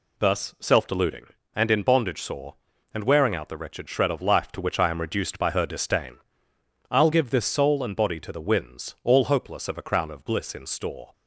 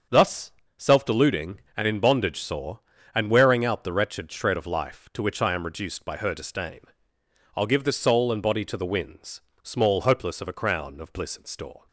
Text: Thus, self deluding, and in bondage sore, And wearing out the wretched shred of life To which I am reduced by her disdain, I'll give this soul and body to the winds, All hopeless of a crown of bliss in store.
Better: first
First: none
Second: starts louder than the rest; until 1.3 s; 6.5 dB // says "Small" for "All"; at 9.6 s

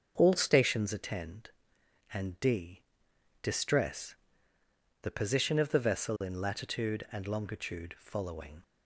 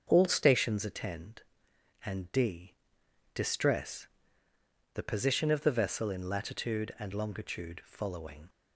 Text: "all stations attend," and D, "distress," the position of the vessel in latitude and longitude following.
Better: neither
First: starts louder than the rest; until 1.1 s; 6.5 dB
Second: starts louder than the rest; until 1.1 s; 6.5 dB

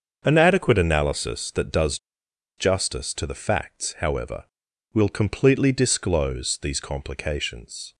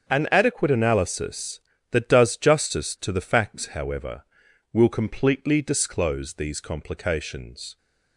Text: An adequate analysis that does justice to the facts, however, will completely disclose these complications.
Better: second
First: starts louder than the rest; until 1.2 s; 6.5 dB // pauses between "does" and "justice"; noticeable; at 1.9 s; 0.61 s long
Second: starts louder than the rest; strong; until 1.1 s; 7.5 dB

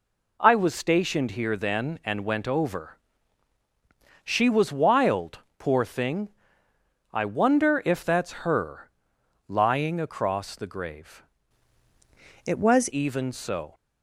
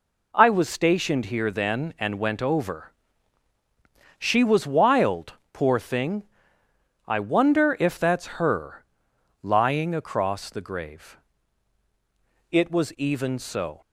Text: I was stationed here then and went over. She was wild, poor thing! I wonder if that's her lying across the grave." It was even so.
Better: second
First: pauses between "her" and "lying"; noticeable; at 8.9 s; 0.56 s long // changes voice from "It" to "was"; from 12.4 to 12.8 s; 0.4 s long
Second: pauses between "her" and "lying"; noticeable; at 8.8 s; 0.56 s long

